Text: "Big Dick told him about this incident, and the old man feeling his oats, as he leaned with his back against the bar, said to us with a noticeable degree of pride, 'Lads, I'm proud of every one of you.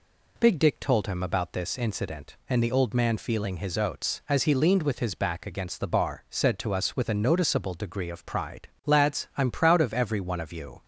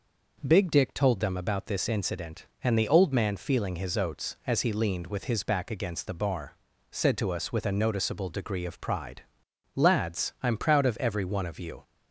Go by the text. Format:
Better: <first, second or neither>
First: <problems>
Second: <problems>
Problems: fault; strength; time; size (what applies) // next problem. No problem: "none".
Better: first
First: none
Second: says "them" for "him"; at 1.1 s